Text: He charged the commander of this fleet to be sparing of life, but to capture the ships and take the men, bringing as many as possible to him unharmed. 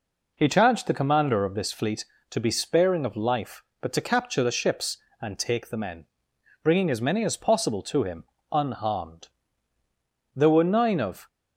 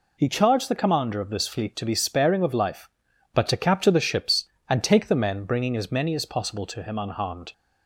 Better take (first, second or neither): second